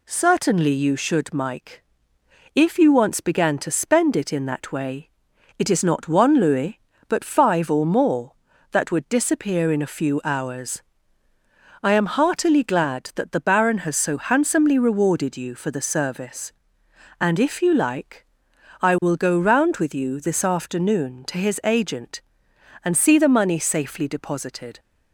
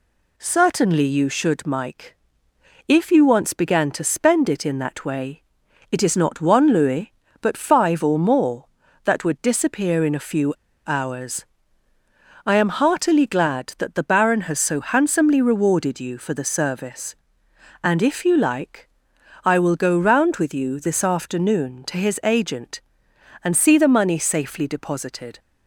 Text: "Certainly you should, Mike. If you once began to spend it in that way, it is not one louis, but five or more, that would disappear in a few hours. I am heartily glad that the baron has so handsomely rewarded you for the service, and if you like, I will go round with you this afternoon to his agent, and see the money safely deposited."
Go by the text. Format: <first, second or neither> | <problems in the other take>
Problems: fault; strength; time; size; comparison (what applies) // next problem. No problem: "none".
first | pauses between "few" and "hours"; slight; at 10.5 s; 0.34 s long